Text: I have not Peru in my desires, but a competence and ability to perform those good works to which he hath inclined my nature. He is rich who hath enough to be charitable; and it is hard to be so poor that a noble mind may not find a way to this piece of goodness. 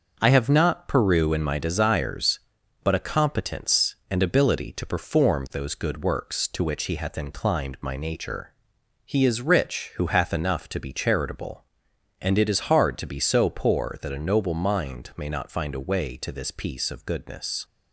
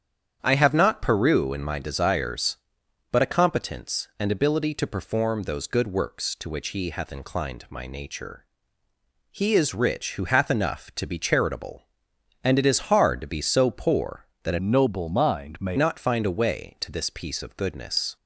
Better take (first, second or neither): first